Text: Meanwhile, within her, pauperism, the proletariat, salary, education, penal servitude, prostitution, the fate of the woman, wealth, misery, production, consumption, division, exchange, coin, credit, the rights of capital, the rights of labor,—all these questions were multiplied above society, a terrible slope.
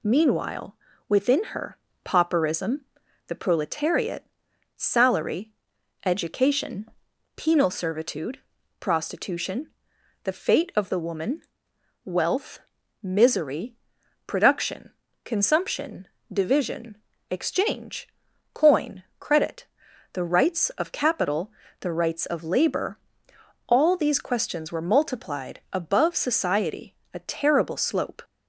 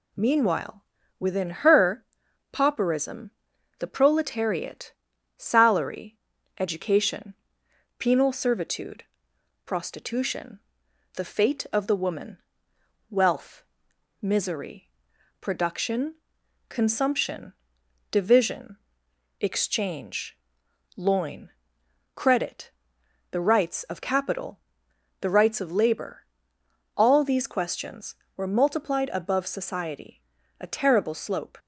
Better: first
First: none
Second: says "loin" for "coin"; at 20.9 s

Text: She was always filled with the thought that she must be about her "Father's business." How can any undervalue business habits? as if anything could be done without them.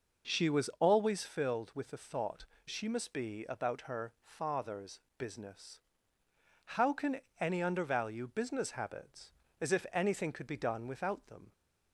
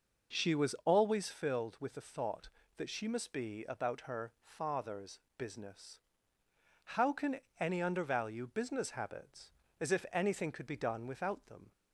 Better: second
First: skips "that"; at 2.5 s // pauses between "Father's" and "business"; slight; at 4.9 s; 0.20 s long // pauses between "can" and "any"; slight; at 7.2 s; 0.18 s long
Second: pauses between "Father's" and "business"; slight; at 5.1 s; 0.20 s long // pauses between "can" and "any"; slight; at 7.3 s; 0.18 s long

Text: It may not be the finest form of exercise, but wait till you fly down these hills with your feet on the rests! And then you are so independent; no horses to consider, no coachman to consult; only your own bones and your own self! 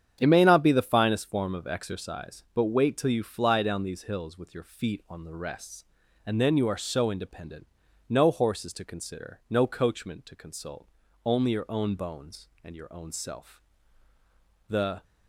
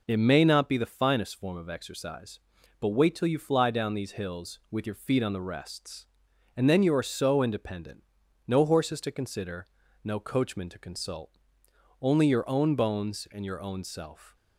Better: second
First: starts louder than the rest; strong; until 1.2 s; 8.5 dB // goes on to say "The"; slight; from 14.6 s on; 0.36 s long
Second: none

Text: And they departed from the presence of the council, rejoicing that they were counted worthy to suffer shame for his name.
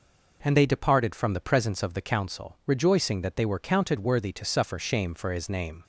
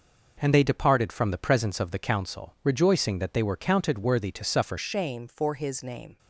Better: first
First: none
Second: changes voice at "shame"; from 4.7 s on; 1.4 s long

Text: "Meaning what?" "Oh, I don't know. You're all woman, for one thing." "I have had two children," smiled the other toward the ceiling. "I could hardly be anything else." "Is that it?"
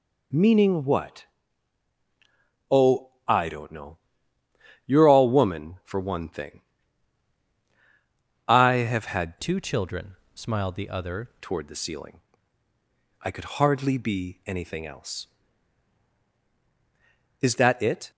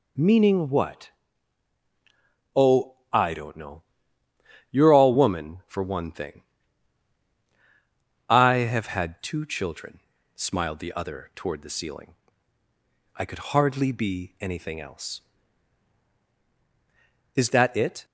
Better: second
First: changes voice from "two" to "other"; from 9.3 to 11.2 s; 1.9 s long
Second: none

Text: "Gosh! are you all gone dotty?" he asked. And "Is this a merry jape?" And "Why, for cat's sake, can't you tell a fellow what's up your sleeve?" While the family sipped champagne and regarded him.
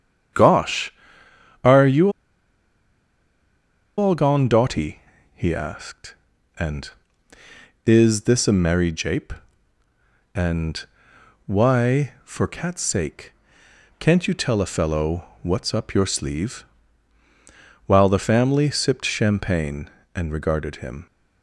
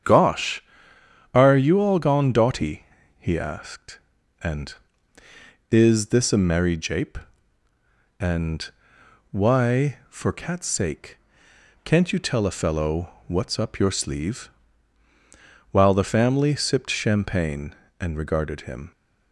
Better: second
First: starts louder than the rest; strong; until 2.0 s; 8 dB // pauses between "you" and "all"; strong; at 2.0 s; 1.8 s long // pauses between "And" and "Why"; noticeable; at 10.8 s; 0.62 s long // pauses between "fellow" and "what's"; slight; at 15.2 s; 0.18 s long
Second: starts louder than the rest; strong; until 1.7 s; 8 dB // pauses between "And" and "Why"; noticeable; at 8.6 s; 0.62 s long // pauses between "fellow" and "what's"; slight; at 13.0 s; 0.18 s long

